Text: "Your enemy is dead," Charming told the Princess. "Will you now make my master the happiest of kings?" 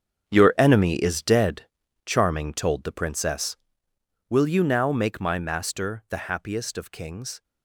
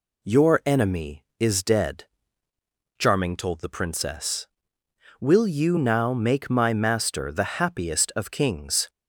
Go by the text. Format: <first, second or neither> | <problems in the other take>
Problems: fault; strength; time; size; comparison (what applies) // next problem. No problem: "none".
second | gets quieter; strong; throughout; 11.5 dB